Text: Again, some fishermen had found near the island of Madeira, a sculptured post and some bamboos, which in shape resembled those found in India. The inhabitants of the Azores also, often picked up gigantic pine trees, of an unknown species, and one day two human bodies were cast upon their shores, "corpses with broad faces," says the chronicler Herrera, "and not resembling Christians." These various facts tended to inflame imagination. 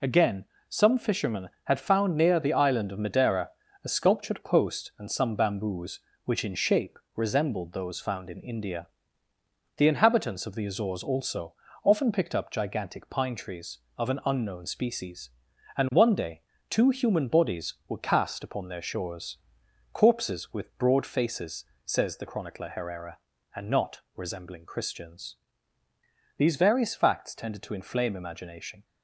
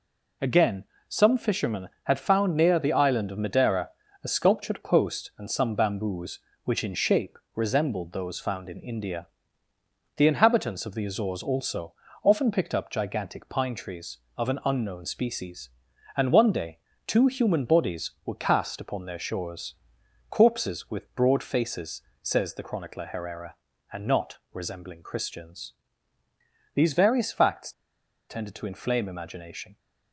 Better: first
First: pauses between "shape" and "resembled"; slight; at 6.9 s; 0.16 s long // pauses between "day" and "two"; slight; at 16.4 s; 0.28 s long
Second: pauses between "shape" and "resembled"; slight; at 7.3 s; 0.16 s long // pauses between "day" and "two"; slight; at 16.7 s; 0.28 s long // pauses between "facts" and "tended"; noticeable; at 27.7 s; 0.57 s long

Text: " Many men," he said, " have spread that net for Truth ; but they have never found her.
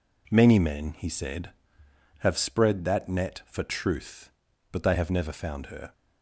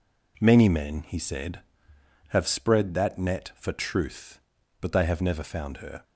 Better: neither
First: none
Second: none

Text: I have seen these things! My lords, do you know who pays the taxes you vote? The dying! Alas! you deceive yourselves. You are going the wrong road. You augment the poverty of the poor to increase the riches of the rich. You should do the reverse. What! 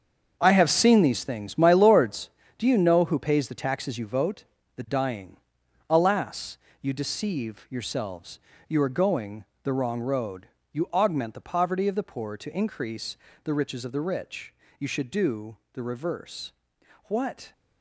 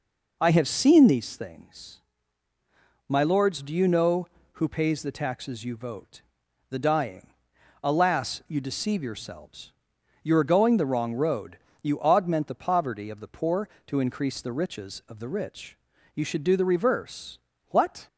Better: second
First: gets quieter; strong; throughout; 11.5 dB // pauses between "going" and "the"; slight; at 9.4 s; 0.20 s long // pauses between "increase" and "the"; slight; at 13.1 s; 0.26 s long // pauses between "do" and "the"; slight; at 15.5 s; 0.16 s long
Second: none

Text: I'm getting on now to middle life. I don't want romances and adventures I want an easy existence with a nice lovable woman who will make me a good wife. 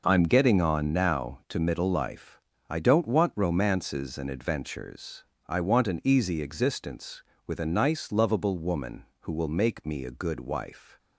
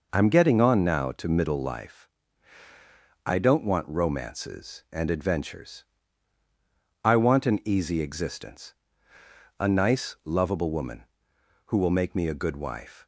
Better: first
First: pauses between "adventures" and "I"; slight; at 5.2 s; 0.22 s long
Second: pauses between "adventures" and "I"; at 5.8 s; 1.1 s long // skips "with"; at 9.1 s

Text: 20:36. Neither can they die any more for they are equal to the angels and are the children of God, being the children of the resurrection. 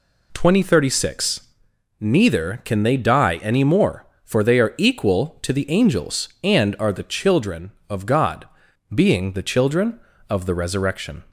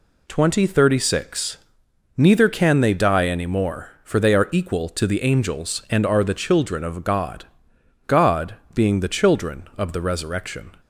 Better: first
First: none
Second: says "God" twice; at 8.0 s

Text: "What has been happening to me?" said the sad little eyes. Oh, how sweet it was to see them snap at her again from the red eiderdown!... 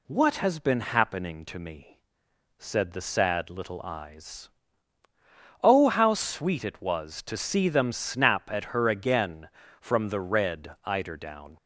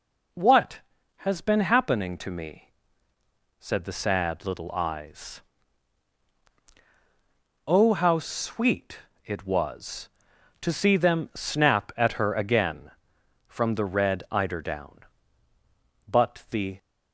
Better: first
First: none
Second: pauses between "sweet" and "it"; slight; at 8.9 s; 0.26 s long // goes on to say "But the"; noticeable; from 16.0 s on; 0.72 s long

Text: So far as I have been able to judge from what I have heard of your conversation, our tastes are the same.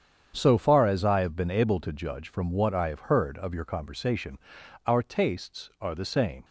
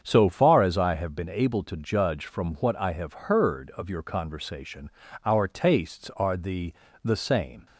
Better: first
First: starts louder than the rest; strong; until 1.3 s; 8 dB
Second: starts louder than the rest; strong; until 1.0 s; 7.5 dB // says "the" twice; at 7.0 s

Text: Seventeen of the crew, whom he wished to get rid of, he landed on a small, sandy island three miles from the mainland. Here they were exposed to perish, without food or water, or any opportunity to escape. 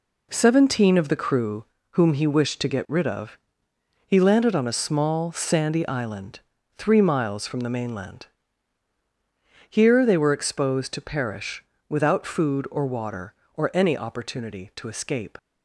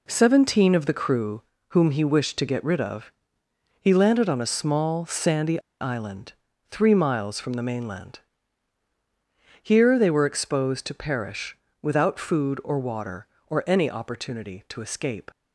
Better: first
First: pauses between "island" and "three"; slight; at 6.3 s; 0.36 s long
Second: pauses between "sandy" and "island"; slight; at 5.6 s; 0.19 s long // pauses between "island" and "three"; slight; at 6.3 s; 0.36 s long

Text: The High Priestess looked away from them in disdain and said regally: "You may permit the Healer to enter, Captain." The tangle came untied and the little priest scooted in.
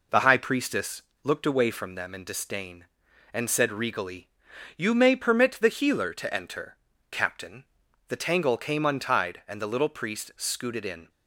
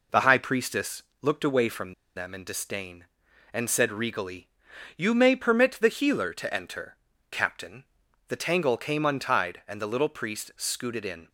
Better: first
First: pauses between "Priestess" and "looked"; slight; at 1.0 s; 0.20 s long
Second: pauses between "Priestess" and "looked"; slight; at 1.0 s; 0.18 s long // pauses between "from" and "them"; slight; at 1.9 s; 0.23 s long

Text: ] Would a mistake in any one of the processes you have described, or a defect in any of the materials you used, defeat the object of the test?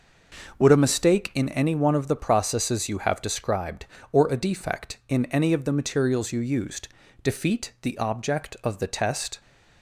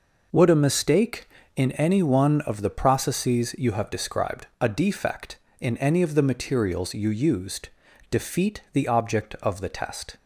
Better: first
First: none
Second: skips "or"; at 4.5 s

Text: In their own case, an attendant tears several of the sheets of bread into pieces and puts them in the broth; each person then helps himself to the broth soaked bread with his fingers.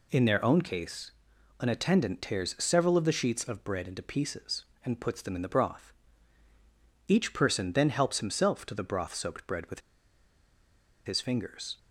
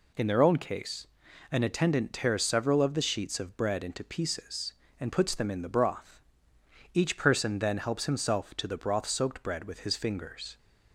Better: second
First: pauses between "with" and "his"; strong; at 9.8 s; 1.2 s long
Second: none

